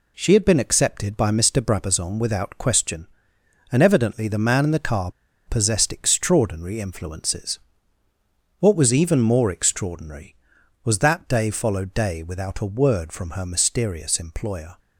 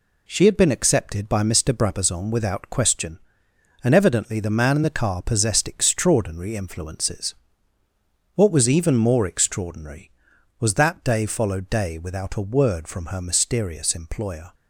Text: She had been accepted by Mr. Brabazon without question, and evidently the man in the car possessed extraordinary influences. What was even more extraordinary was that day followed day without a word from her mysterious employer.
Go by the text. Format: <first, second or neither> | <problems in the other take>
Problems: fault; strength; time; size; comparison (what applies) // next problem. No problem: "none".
second | pauses between "car" and "possessed"; at 5.1 s; 0.36 s long